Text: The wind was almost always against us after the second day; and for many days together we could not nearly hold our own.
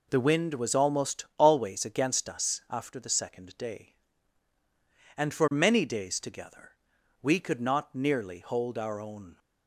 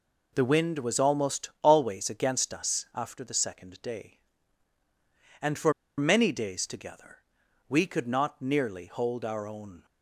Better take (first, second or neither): first